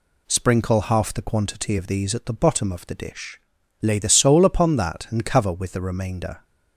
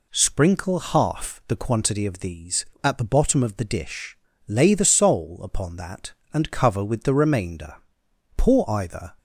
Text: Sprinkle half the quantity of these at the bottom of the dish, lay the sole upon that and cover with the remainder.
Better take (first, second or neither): first